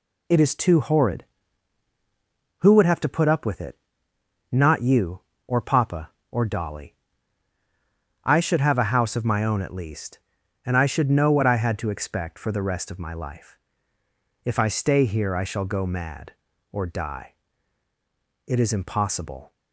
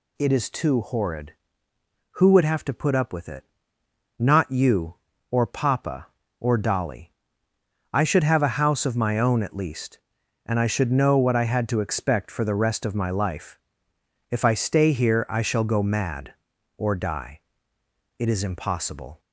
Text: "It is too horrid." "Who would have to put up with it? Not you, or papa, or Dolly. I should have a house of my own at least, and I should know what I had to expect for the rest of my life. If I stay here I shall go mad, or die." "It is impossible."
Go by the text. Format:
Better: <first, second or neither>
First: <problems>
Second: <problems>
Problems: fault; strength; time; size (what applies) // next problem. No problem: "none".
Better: neither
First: none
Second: none